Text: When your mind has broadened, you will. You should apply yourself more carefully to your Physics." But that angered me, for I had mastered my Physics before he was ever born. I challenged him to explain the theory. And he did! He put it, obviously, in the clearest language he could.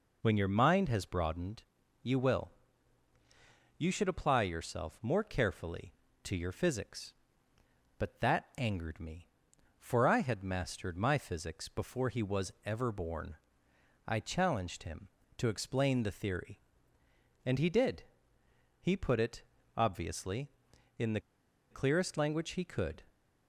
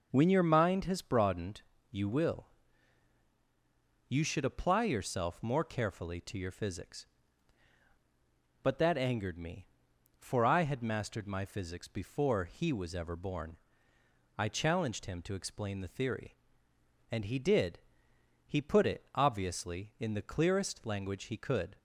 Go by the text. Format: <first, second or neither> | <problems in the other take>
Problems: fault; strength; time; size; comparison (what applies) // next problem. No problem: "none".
second | pauses between "the" and "clearest"; noticeable; at 21.2 s; 0.49 s long